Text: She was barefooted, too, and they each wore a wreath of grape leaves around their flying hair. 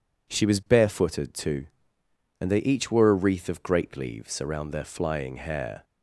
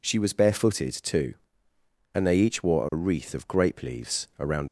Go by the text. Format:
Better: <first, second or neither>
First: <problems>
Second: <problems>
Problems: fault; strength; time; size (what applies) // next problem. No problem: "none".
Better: first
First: none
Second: stops before "their flying hair"; at 4.6 s